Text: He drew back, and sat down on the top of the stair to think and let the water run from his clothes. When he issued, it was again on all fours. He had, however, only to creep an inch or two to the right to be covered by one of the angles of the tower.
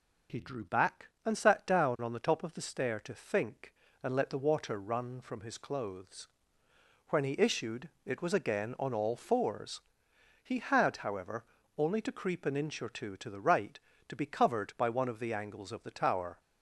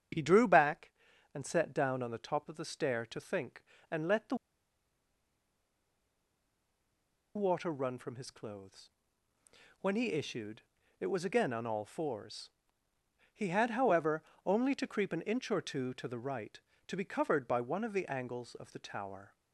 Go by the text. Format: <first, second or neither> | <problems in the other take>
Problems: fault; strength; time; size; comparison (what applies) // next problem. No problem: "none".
first | starts louder than the rest; strong; until 1.5 s; 7.5 dB // pauses between "the" and "water"; strong; at 4.3 s; 3.0 s long